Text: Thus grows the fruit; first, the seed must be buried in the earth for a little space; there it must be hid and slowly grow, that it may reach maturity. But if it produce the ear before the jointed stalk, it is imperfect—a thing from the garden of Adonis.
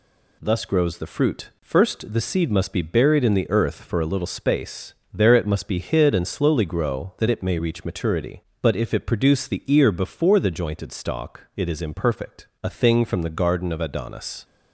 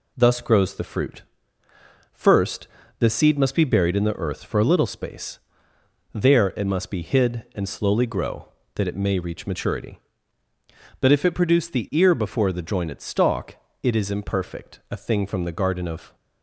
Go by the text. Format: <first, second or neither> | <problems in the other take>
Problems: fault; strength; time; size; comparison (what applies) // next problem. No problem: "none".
first | stops before "Adonis"; at 16.1 s